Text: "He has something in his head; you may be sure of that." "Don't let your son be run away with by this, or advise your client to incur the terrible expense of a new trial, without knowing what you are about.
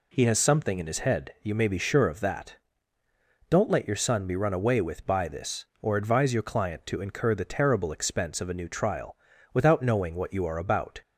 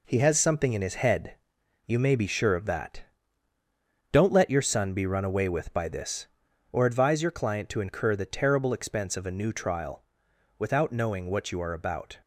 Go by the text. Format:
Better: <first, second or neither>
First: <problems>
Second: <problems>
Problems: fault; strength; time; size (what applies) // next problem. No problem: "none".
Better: first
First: none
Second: gets quieter; throughout; 6.5 dB